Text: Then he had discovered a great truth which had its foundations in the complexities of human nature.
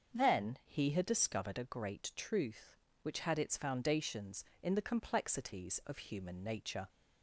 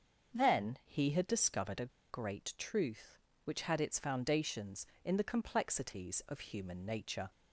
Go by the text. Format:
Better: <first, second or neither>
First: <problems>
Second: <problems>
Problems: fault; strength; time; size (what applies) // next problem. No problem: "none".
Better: first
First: starts louder than the rest; until 1.2 s; 6.5 dB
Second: starts louder than the rest; until 1.4 s; 6.5 dB // pauses between "a" and "great"; slight; at 1.9 s; 0.20 s long